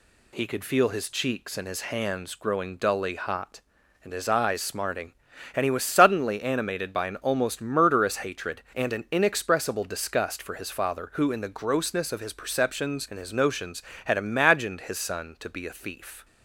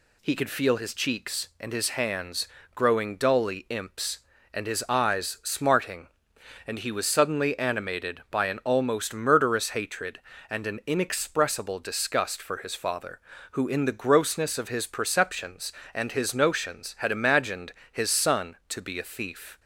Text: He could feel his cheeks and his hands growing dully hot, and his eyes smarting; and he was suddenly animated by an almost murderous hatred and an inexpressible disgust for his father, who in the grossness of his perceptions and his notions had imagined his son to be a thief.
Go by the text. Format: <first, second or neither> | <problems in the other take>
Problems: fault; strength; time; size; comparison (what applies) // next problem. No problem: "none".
first | pauses between "hands" and "growing"; slight; at 2.4 s; 0.26 s long // says "imps" for "hot"; at 3.6 s // pauses between "imagined" and "his"; slight; at 17.7 s; 0.20 s long